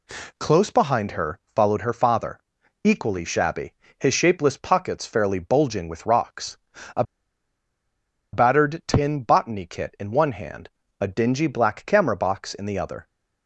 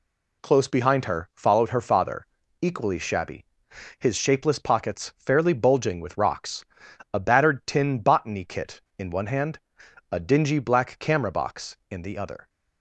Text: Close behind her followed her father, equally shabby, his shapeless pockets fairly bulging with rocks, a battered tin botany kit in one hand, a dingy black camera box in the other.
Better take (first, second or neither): second